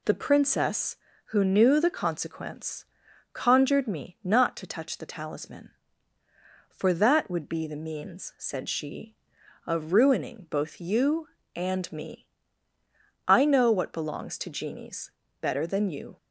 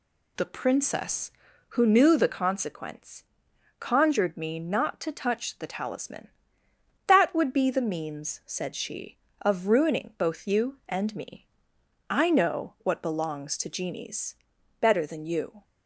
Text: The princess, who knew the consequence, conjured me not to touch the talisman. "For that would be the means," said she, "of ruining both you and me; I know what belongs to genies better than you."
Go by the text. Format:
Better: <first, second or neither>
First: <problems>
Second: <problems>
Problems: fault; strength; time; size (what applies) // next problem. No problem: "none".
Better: first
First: pauses between "genies" and "better"; slight; at 15.1 s; 0.30 s long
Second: skips "For"; at 6.6 s // pauses between "genies" and "better"; noticeable; at 14.3 s; 0.46 s long